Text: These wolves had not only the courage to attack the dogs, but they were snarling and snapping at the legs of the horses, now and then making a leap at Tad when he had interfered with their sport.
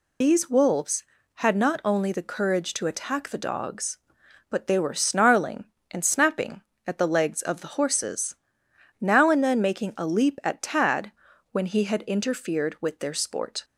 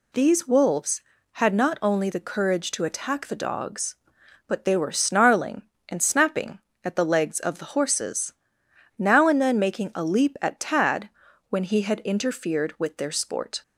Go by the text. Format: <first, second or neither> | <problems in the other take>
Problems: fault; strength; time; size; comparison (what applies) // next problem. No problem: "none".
second | loses the start of "These"; at 0.2 s; 40 ms // pauses between "Tad" and "when"; at 11.1 s; 0.40 s long; also in the second